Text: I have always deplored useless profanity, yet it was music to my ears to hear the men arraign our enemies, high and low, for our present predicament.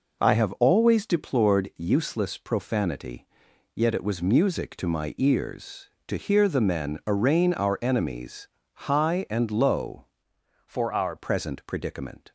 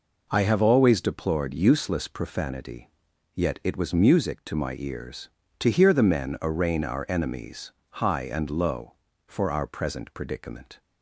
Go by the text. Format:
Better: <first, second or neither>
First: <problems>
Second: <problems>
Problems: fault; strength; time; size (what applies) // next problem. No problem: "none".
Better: second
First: changes voice from "for" to "our"; from 10.6 to 11.1 s; 0.5 s long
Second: none